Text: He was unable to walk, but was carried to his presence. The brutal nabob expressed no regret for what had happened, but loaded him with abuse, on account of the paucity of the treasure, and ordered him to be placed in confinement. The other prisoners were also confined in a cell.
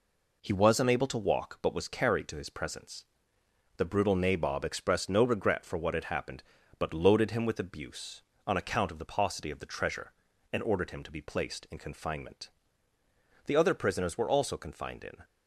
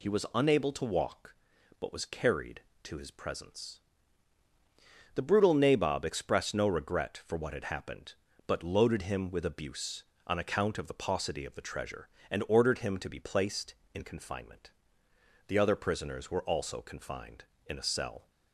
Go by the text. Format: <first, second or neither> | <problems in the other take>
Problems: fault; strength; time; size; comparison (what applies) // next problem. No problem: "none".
second | stops before "a cell"; at 15.2 s